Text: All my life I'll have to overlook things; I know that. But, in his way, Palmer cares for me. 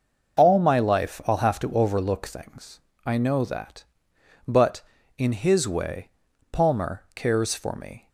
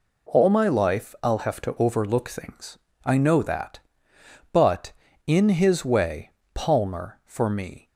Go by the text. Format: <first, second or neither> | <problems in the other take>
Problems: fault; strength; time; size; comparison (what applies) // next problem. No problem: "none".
first | skips "cares"; at 7.2 s